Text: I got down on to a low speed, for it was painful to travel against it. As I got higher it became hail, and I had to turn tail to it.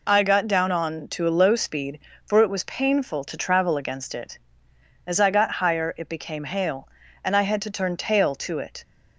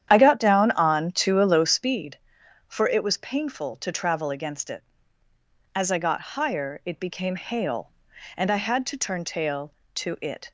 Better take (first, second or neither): first